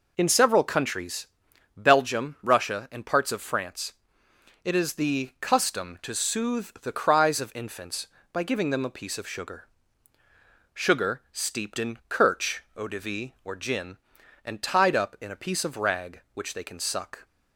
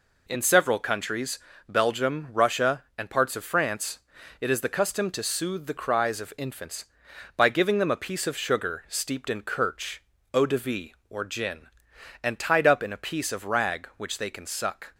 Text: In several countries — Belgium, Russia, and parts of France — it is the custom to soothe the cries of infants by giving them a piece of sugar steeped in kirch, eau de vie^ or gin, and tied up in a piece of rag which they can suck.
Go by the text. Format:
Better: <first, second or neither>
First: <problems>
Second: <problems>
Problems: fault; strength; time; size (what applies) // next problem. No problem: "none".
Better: second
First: says "sugar" twice; at 10.7 s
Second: none